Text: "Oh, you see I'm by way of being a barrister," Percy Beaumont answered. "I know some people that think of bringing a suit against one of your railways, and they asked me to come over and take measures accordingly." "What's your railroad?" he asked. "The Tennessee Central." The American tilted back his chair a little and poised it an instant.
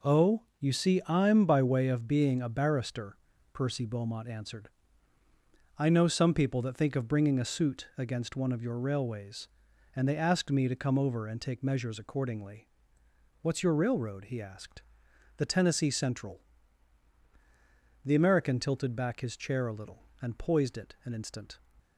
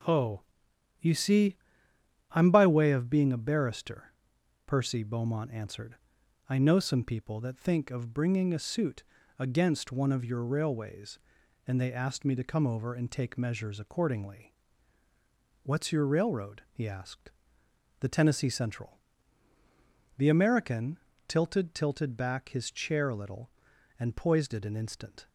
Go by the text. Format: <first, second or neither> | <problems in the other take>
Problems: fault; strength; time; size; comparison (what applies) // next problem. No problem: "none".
first | pauses between "see" and "I'm"; noticeable; at 1.5 s; 0.76 s long // pauses between "suit" and "against"; slight; at 9.0 s; 0.34 s long // pauses between "American" and "tilted"; slight; at 20.9 s; 0.30 s long // says "tilted" twice; at 21.7 s